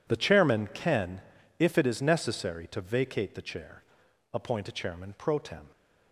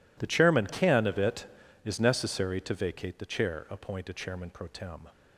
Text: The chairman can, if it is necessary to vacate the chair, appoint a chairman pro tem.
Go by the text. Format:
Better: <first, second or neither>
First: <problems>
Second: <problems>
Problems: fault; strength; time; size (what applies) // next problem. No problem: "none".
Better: first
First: none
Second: says "of" for "if"; at 1.0 s